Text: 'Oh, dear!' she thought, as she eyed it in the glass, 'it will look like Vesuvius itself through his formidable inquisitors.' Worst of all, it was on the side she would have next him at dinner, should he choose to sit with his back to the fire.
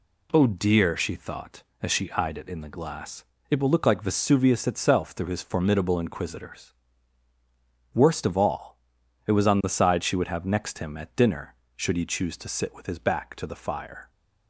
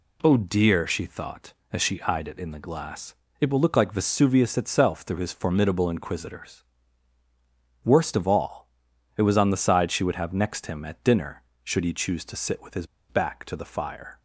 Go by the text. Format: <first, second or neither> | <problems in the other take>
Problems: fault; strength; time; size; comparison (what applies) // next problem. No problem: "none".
first | pauses between "his" and "back"; slight; at 12.8 s; 0.24 s long